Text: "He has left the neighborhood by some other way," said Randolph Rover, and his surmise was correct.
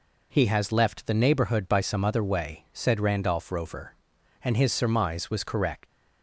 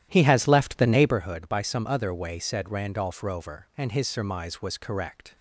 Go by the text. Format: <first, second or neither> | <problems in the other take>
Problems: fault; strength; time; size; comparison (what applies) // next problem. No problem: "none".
first | starts louder than the rest; strong; until 1.2 s; 12 dB